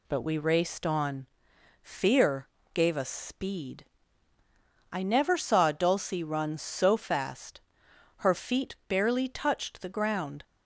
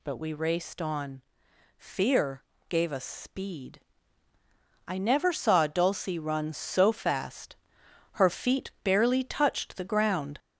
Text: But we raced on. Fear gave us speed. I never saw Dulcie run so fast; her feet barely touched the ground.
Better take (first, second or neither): first